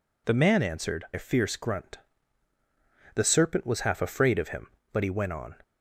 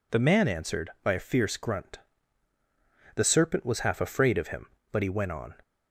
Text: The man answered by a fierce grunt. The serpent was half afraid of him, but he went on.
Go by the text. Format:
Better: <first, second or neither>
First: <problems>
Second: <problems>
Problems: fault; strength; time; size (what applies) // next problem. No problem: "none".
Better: second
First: skips "by"; at 1.0 s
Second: none